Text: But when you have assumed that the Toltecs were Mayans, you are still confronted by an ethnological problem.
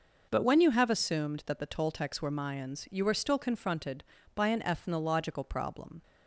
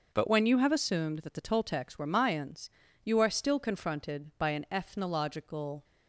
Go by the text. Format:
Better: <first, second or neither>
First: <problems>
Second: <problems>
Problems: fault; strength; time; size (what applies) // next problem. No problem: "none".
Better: first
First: none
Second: stops before "problem"; at 5.8 s